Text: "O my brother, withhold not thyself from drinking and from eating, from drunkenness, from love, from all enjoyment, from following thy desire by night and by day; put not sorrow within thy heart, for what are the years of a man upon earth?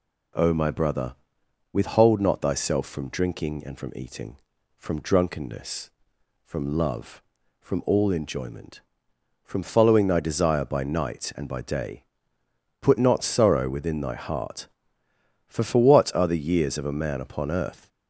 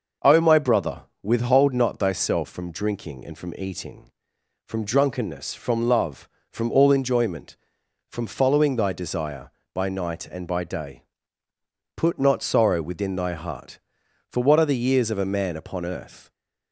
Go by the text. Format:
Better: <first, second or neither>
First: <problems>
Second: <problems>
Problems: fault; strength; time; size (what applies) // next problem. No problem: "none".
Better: second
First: says "for" twice; at 15.6 s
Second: none